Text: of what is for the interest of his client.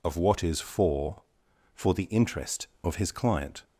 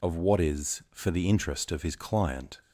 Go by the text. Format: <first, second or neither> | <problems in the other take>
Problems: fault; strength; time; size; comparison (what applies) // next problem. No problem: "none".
second | says "for" twice; at 1.7 s